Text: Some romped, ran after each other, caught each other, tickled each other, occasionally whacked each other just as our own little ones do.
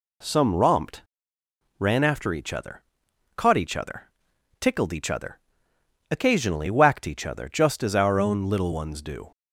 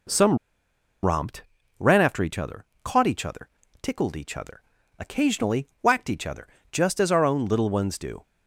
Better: first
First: none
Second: pauses between "Some" and "romped"; noticeable; at 0.3 s; 0.67 s long // pauses between "occasionally" and "whacked"; slight; at 5.6 s; 0.16 s long // pauses between "other" and "just"; slight; at 6.4 s; 0.24 s long

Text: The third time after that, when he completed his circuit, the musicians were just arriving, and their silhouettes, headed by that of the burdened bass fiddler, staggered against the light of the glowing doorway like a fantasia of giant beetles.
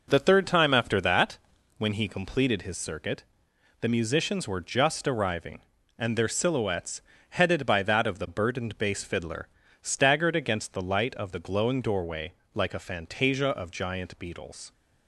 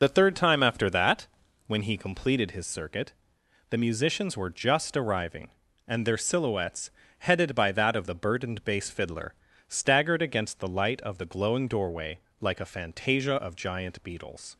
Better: first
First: pauses between "doorway" and "like"; slight; at 12.3 s; 0.24 s long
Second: loses the start of "The"; at 0.0 s; 40 ms // pauses between "doorway" and "like"; slight; at 12.1 s; 0.24 s long

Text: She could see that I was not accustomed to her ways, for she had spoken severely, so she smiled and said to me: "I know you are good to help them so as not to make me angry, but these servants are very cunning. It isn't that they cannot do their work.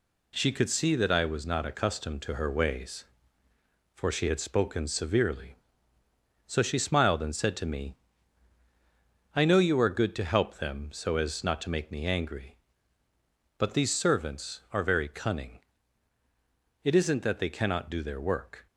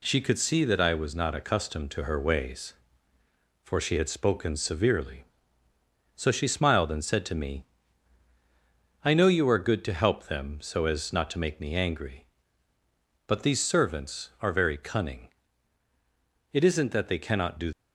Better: first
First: none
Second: stops before "their work"; at 17.7 s

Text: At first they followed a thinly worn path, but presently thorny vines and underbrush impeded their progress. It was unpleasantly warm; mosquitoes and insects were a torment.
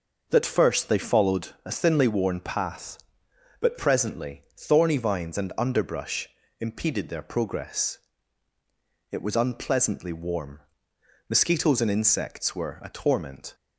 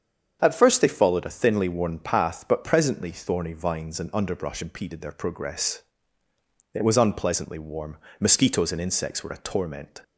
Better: second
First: starts louder than the rest; noticeable; until 1.3 s; 6 dB // says "That" for "At"; at 0.2 s // pauses between "presently" and "thorny"; slight; at 4.4 s; 0.16 s long // pauses between "underbrush" and "impeded"; slight; at 6.2 s; 0.30 s long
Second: starts louder than the rest; strong; until 1.4 s; 7.5 dB

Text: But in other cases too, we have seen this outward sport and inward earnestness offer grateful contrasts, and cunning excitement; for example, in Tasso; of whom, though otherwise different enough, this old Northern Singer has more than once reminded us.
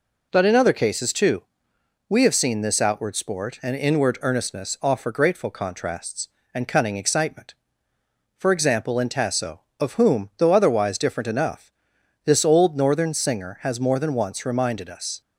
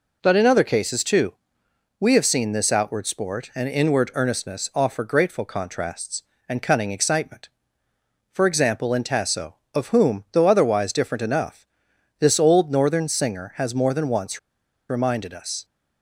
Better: first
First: none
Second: pauses between "once" and "reminded"; noticeable; at 14.3 s; 0.50 s long

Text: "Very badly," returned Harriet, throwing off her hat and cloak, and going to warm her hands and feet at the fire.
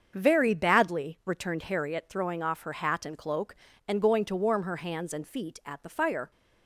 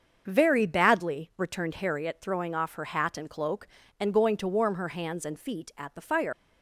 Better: first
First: starts louder than the rest; until 1.1 s; 7 dB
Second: starts louder than the rest; until 1.2 s; 6.5 dB // leaves "fire" unfinished; at 6.3 s; 95 ms

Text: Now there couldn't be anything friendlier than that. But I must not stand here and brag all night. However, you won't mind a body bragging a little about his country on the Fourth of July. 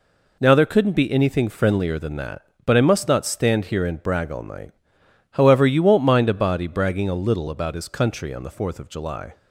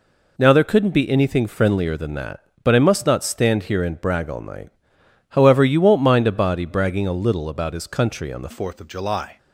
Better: first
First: none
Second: changes voice at "Fourth"; from 8.5 s on; 0.8 s long

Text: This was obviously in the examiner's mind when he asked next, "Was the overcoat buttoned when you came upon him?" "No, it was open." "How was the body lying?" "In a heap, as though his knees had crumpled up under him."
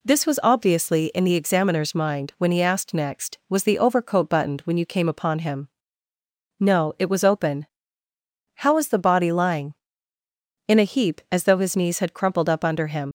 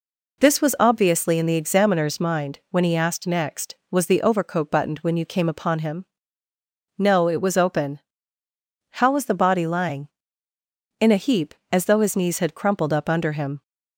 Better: second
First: leaves "him" unfinished; at 13.0 s; 75 ms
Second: none

